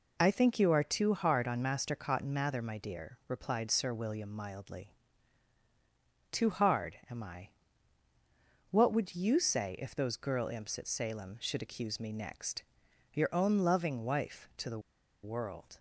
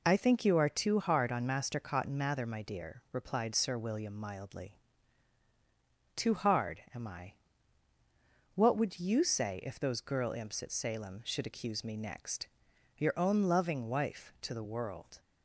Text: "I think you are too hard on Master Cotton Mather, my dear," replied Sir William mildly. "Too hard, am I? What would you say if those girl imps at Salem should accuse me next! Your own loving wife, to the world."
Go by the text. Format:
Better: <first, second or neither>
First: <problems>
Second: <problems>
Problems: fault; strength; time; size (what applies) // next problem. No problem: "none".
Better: second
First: pauses between "the" and "world"; at 14.7 s; 0.44 s long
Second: none